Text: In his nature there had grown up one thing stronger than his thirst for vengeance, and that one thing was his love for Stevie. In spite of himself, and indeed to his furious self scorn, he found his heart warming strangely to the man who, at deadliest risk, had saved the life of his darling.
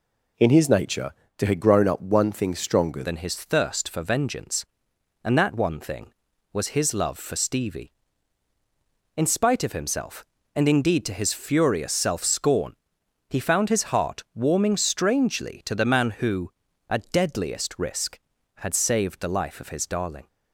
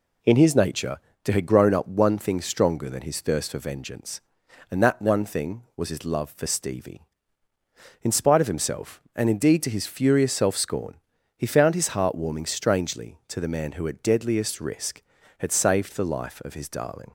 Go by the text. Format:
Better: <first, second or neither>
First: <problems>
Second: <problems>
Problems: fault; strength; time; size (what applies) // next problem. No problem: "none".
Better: second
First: pauses between "nature" and "there"; slight; at 1.1 s; 0.24 s long // changes voice at "than"; from 3.0 s on; 17.2 s long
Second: pauses between "nature" and "there"; slight; at 0.9 s; 0.24 s long